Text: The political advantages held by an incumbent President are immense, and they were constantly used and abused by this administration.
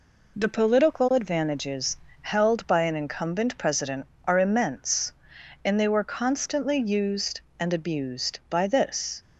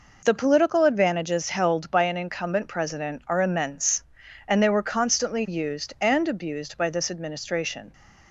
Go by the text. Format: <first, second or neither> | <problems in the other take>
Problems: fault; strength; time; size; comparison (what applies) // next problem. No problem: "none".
second | pauses between "advantages" and "held"; slight; at 1.9 s; 0.28 s long // stops before "administration"; at 9.2 s